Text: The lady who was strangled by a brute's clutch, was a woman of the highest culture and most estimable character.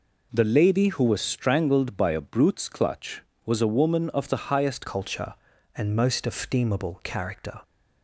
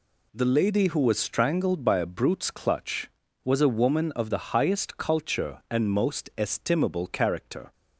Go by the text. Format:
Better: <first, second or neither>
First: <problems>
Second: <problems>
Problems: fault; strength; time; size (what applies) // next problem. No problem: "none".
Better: second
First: changes voice at "culture"; from 4.8 s on; 2.8 s long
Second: none